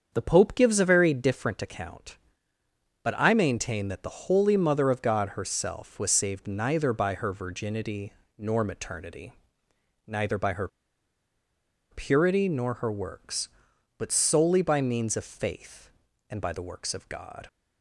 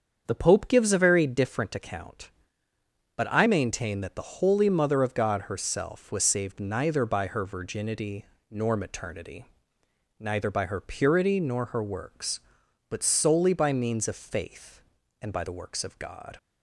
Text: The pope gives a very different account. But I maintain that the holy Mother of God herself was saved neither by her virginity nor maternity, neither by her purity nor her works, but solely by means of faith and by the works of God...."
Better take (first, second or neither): second